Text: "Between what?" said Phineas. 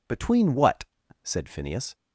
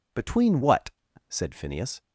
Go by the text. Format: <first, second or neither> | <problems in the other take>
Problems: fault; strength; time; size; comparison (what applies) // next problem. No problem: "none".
neither | none